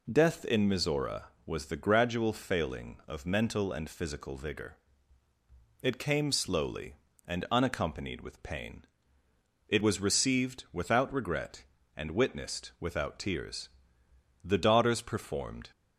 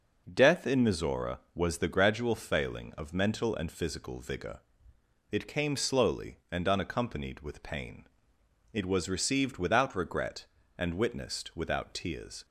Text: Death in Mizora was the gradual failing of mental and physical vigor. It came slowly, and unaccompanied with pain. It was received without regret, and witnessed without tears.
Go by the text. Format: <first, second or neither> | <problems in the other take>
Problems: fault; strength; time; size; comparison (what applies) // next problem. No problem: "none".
second | goes on to say "The daughters performed"; noticeable; from 14.4 s on; 1.2 s long